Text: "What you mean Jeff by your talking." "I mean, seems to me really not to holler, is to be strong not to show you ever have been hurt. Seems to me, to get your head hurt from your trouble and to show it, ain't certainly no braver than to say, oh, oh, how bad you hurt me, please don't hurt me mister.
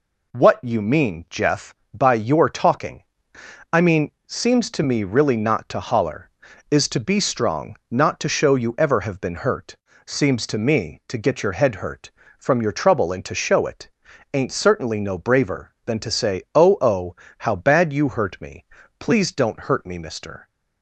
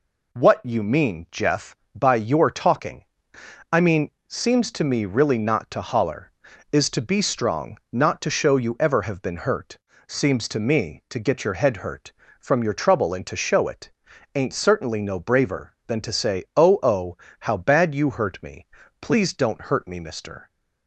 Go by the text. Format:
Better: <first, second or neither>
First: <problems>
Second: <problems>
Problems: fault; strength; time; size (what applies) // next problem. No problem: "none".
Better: neither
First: none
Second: none